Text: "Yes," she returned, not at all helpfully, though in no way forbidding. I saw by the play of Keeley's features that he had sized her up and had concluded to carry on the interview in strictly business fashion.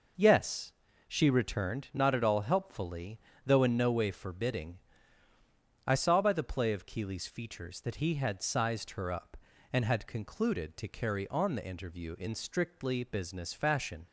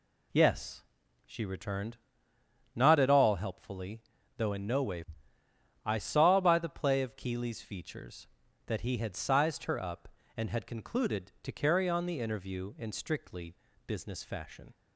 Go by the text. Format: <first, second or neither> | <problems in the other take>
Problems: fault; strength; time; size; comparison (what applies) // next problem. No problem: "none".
first | skips "forbidding"; at 5.4 s // pauses between "strictly" and "business"; slight; at 13.5 s; 0.30 s long